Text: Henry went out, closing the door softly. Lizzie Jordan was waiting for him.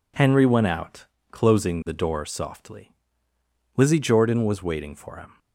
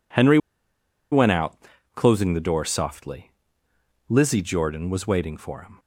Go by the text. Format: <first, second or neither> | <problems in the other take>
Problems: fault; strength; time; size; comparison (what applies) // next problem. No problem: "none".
first | pauses between "Henry" and "went"; noticeable; at 0.3 s; 0.74 s long